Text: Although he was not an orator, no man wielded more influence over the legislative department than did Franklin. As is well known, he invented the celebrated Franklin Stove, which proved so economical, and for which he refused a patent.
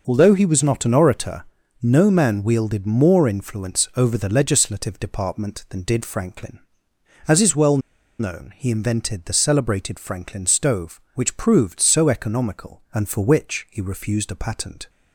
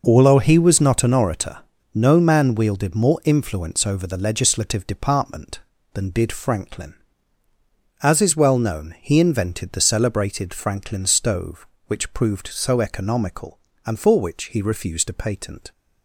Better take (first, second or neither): second